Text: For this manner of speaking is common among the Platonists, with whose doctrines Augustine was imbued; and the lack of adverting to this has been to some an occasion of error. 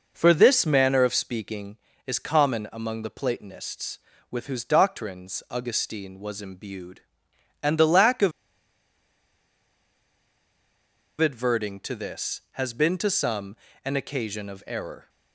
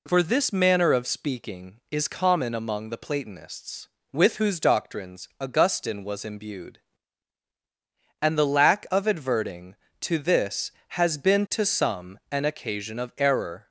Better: second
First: pauses between "of" and "adverting"; strong; at 8.3 s; 2.8 s long // pauses between "some" and "an"; slight; at 13.5 s; 0.26 s long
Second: none

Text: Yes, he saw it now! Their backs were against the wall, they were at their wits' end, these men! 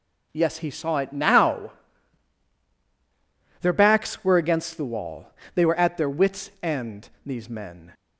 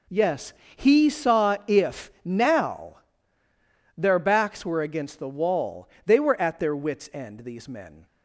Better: first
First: none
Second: says "if" for "it"; at 1.6 s

